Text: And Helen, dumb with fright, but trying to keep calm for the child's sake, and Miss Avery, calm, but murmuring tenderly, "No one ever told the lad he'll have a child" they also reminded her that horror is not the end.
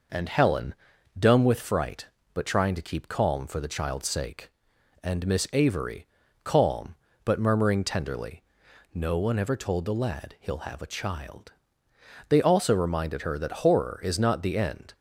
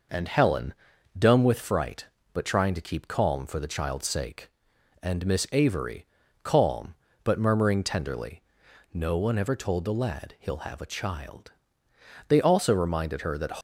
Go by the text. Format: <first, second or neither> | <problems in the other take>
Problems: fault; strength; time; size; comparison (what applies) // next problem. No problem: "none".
first | pauses between "child" and "they"; noticeable; at 11.5 s; 0.74 s long; noticeable in the first // stops before "horror is not the end"; at 13.5 s